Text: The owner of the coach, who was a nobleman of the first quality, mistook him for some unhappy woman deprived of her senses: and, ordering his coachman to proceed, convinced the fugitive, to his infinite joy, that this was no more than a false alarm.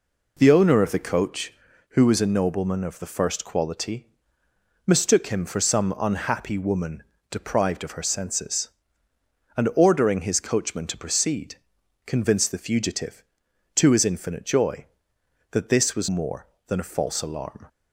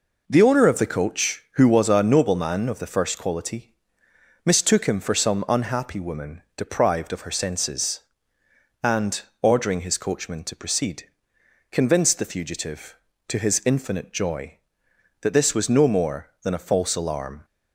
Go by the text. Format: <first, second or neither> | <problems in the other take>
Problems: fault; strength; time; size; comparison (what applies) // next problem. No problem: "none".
second | pauses between "woman" and "deprived"; slight; at 7.0 s; 0.30 s long // skips "no"; at 16.0 s